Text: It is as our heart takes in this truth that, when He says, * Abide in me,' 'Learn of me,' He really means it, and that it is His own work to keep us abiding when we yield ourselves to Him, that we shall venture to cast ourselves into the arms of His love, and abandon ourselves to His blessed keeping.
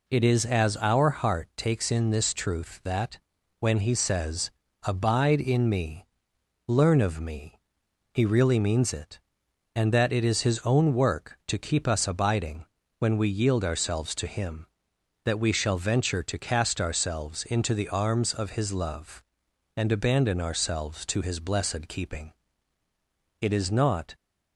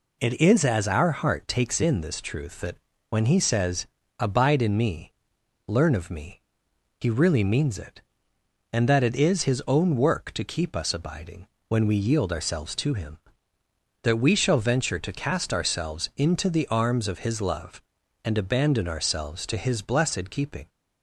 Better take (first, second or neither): second